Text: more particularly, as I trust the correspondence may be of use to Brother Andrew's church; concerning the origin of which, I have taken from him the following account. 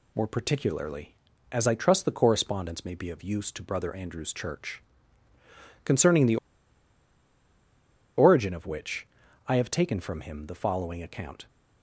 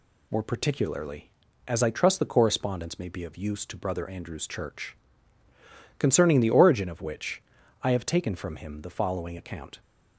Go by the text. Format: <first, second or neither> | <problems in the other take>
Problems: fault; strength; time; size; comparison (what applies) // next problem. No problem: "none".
second | pauses between "the" and "origin"; strong; at 6.3 s; 1.8 s long